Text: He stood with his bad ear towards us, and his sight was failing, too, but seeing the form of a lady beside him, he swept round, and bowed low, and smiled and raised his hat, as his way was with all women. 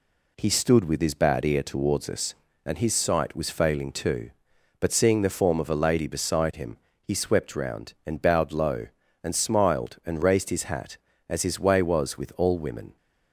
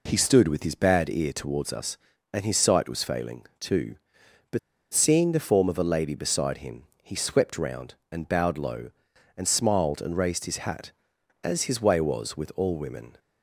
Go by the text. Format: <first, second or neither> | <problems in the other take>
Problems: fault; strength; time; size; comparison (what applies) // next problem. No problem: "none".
first | pauses between "but" and "seeing"; slight; at 4.5 s; 0.34 s long